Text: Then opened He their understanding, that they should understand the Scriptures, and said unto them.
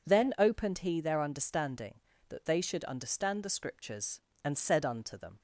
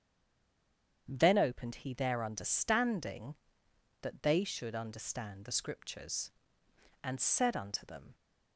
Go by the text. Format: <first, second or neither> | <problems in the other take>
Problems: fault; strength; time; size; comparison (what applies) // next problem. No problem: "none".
first | stays silent before the first word; until 1.0 s; 1.0 s long // starts louder than the rest; strong; until 2.0 s; 8 dB